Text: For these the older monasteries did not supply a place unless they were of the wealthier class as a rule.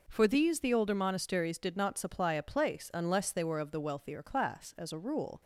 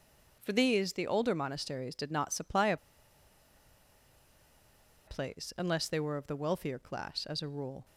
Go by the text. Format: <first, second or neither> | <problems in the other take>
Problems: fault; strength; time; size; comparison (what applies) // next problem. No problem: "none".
first | pauses between "a" and "place"; strong; at 2.7 s; 2.3 s long